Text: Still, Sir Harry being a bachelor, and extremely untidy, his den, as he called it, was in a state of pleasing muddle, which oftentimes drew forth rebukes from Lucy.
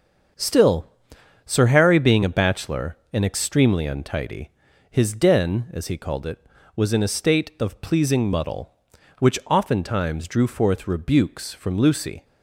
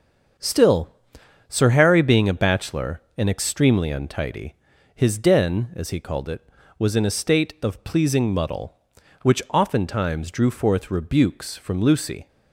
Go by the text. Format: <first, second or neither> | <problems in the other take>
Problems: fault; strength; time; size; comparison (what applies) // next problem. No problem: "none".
neither | starts louder than the rest; the same in both